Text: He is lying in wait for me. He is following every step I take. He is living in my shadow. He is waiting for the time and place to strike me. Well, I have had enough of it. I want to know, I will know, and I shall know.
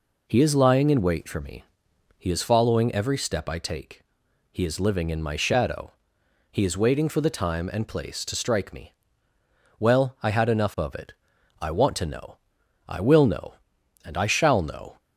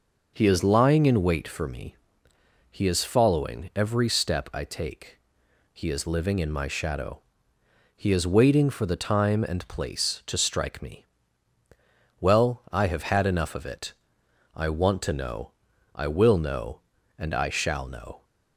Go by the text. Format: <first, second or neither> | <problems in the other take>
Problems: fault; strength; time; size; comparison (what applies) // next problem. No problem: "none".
second | skips "have"; at 10.3 s